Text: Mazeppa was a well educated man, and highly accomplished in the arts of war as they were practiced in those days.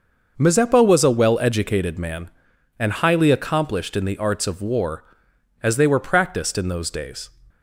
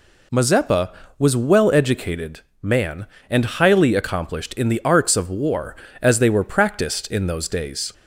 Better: first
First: none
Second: skips "a"; at 1.3 s // pauses between "educated" and "man"; slight; at 2.4 s; 0.22 s long

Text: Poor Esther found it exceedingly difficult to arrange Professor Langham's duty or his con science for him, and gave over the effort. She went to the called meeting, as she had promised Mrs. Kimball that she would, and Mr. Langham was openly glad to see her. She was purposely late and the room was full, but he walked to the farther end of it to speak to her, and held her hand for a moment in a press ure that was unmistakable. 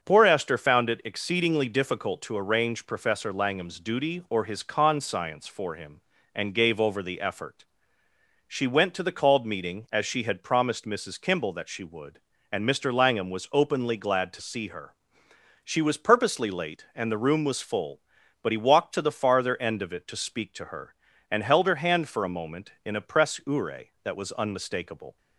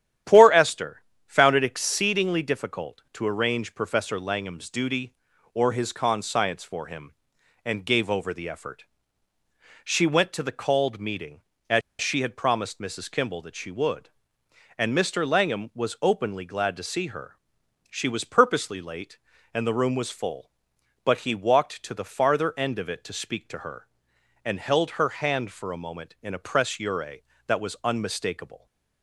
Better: first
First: starts louder than the rest; strong; until 1.0 s; 7 dB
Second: starts louder than the rest; strong; until 1.5 s; 10.5 dB // pauses between "Esther" and "found"; slight; at 1.0 s; 0.24 s long // pauses between "as" and "she"; slight; at 11.8 s; 0.20 s long

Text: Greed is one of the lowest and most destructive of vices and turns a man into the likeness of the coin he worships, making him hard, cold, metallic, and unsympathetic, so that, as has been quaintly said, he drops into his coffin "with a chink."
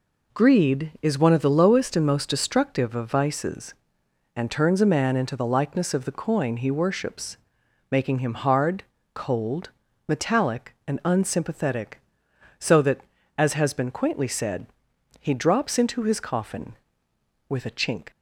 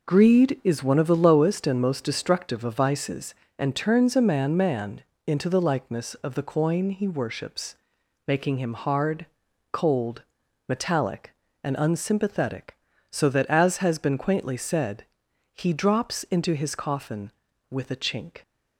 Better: first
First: none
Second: says "man" twice; at 4.5 s

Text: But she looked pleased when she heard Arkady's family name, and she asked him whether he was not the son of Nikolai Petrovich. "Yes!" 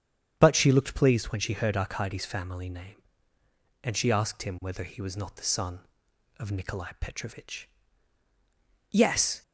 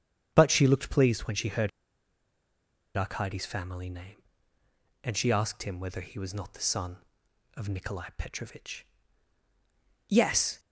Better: first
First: starts louder than the rest; strong; until 1.3 s; 8.5 dB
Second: starts louder than the rest; strong; until 1.3 s; 8.5 dB // pauses between "heard" and "Arkady's"; strong; at 1.6 s; 1.2 s long

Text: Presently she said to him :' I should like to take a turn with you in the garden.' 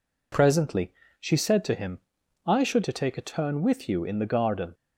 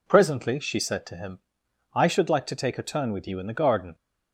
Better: second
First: pauses between "Presently" and "she"; slight; at 0.9 s; 0.28 s long // skips "like"; at 2.8 s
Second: none

